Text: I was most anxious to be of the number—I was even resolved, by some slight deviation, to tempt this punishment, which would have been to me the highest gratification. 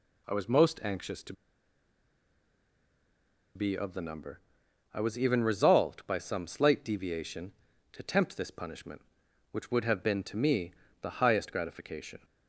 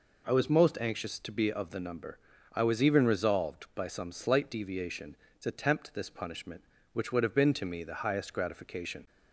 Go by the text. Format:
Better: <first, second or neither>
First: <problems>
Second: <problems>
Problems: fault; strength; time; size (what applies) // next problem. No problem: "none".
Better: second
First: pauses between "to" and "be"; strong; at 1.3 s; 2.2 s long // pauses between "me" and "the"; slight; at 10.7 s; 0.28 s long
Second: none